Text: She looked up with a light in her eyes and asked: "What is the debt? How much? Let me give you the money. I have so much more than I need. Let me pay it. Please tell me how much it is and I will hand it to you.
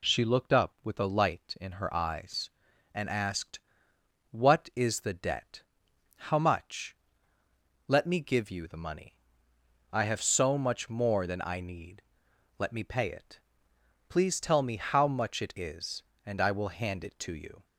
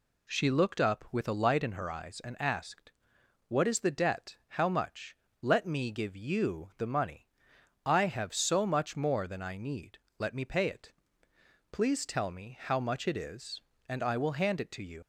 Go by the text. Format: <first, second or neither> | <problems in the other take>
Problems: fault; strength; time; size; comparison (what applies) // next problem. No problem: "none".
first | leaves "you" unfinished; at 15.0 s; 95 ms